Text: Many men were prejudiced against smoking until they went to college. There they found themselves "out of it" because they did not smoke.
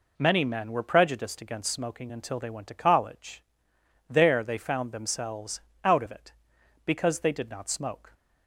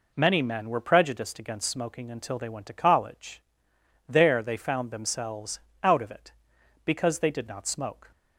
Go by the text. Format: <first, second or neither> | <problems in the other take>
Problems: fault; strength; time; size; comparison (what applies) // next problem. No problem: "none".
neither | pauses between "themselves" and "out"; slight; the same in both